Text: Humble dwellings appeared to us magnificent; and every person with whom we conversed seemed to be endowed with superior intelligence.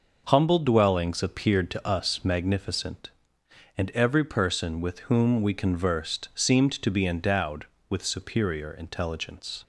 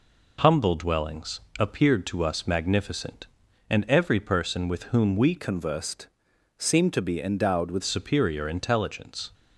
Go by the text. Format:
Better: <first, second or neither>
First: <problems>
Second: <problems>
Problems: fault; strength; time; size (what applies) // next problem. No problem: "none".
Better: first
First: none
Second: pauses between "dwellings" and "appeared"; slight; at 1.4 s; 0.18 s long // changes voice from "conversed" to "with"; from 5.3 to 7.8 s; 2.5 s long // pauses between "conversed" and "seemed"; noticeable; at 6.0 s; 0.52 s long